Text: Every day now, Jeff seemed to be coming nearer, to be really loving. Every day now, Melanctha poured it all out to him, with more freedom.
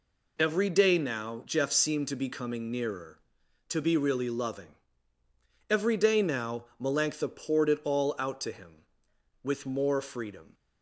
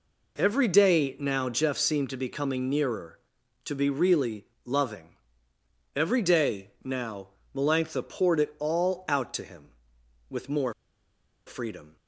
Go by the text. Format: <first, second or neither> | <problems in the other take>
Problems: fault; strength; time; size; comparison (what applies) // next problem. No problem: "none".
first | pauses between "really" and "loving"; slight; at 4.4 s; 0.22 s long // pauses between "day" and "now"; slight; at 6.6 s; 0.16 s long // pauses between "more" and "freedom"; noticeable; at 10.7 s; 0.74 s long